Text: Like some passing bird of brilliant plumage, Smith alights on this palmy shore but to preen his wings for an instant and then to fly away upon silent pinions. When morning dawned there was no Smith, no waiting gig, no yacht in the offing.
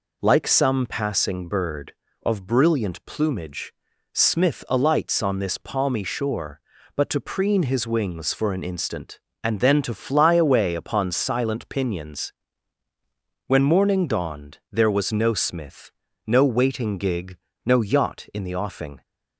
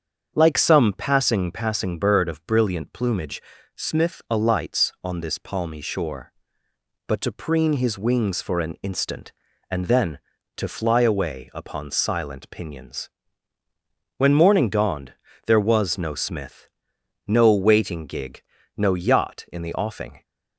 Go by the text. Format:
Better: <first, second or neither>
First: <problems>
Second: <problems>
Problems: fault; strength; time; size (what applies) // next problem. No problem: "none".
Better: first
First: none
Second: starts louder than the rest; strong; until 1.3 s; 7 dB // says "passing" twice; at 1.5 s // pauses between "dawned" and "there"; slight; at 15.1 s; 0.32 s long